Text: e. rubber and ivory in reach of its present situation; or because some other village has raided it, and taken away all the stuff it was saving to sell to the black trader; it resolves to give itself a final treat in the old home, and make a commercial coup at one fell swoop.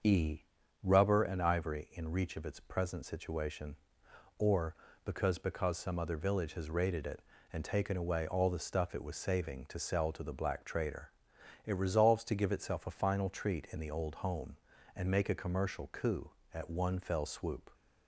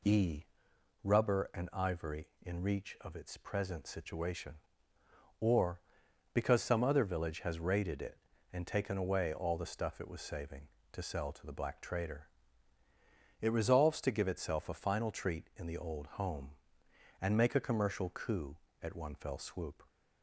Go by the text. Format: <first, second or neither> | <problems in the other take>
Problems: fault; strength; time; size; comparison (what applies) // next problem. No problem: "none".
second | starts louder than the rest; until 1.4 s; 6.5 dB // says "because" twice; at 5.3 s